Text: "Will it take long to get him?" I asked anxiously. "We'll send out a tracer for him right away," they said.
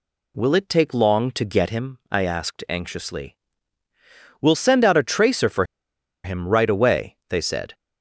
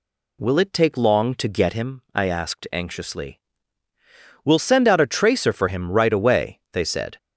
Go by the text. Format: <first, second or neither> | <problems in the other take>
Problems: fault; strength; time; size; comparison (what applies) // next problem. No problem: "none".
second | pauses between "for" and "him"; noticeable; at 5.6 s; 0.60 s long